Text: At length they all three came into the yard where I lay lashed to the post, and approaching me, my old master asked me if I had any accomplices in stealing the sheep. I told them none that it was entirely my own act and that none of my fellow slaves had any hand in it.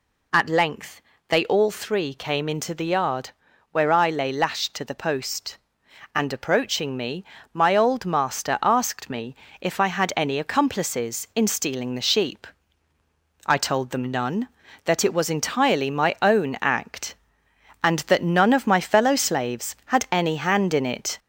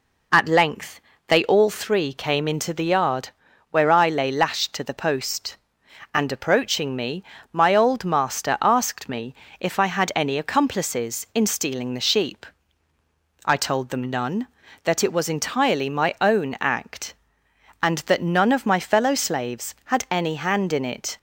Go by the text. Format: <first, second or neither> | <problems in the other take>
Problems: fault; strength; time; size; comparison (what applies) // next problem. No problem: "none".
second | gets louder; slight; throughout; 2.5 dB // pauses between "length" and "they"; slight; at 1.0 s; 0.28 s long; slight in the second // pauses between "yard" and "where"; at 3.3 s; 0.42 s long; also in the second // pauses between "me" and "if"; slight; at 9.3 s; 0.26 s long; slight in the second